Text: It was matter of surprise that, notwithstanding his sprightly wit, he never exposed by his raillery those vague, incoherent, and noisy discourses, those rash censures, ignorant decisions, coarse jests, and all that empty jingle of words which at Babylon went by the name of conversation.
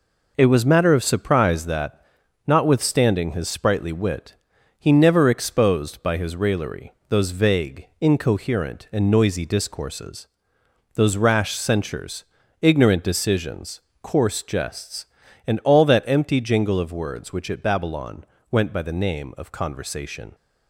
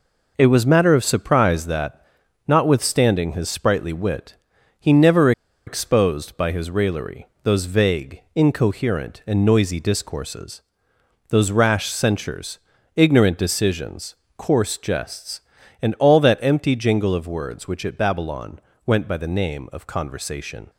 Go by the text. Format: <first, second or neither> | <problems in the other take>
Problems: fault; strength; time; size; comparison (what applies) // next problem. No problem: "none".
first | pauses between "never" and "exposed"; slight; at 5.3 s; 0.35 s long // pauses between "raillery" and "those"; slight; at 7.2 s; 0.18 s long; slight in the first // pauses between "Babylon" and "went"; slight; at 18.5 s; 0.26 s long; slight in the first